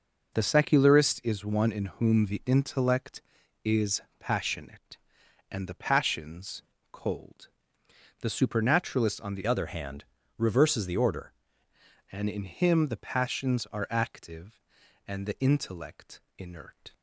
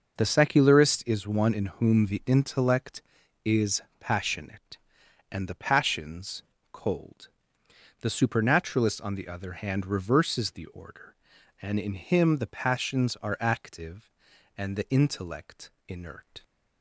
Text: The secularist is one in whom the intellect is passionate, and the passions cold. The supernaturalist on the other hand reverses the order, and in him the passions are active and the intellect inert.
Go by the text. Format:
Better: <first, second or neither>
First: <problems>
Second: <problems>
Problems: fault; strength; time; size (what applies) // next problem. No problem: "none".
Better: second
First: pauses between "is" and "passionate"; slight; at 4.0 s; 0.18 s long // pauses between "passions" and "cold"; slight; at 6.6 s; 0.28 s long // changes voice from "other" to "order"; from 9.4 to 11.3 s; 1.9 s long // pauses between "hand" and "reverses"; slight; at 10.0 s; 0.34 s long // pauses between "intellect" and "inert"; slight; at 16.2 s; 0.16 s long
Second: pauses between "is" and "passionate"; slight; at 3.8 s; 0.18 s long // pauses between "passions" and "cold"; slight; at 6.4 s; 0.28 s long // pauses between "intellect" and "inert"; slight; at 15.7 s; 0.16 s long